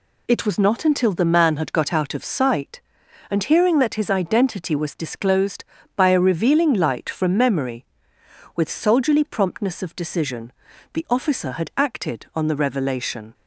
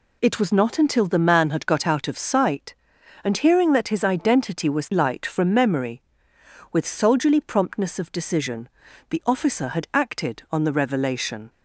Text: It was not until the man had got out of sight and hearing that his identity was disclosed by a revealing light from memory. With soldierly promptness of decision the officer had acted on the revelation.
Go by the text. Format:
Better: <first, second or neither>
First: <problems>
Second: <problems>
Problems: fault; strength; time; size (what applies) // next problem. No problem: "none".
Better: first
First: pauses between "decision" and "the"; at 10.5 s; 0.40 s long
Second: skips "disclosed by a revealing"; at 4.9 s // pauses between "decision" and "the"; at 8.6 s; 0.40 s long